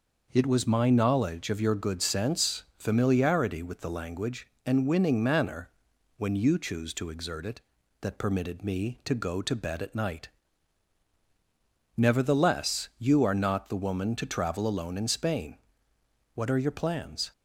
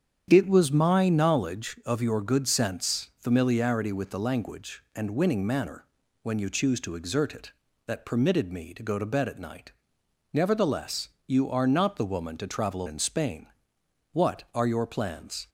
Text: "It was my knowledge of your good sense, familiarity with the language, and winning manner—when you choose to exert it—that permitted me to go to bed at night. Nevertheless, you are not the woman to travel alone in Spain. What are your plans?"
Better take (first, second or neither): first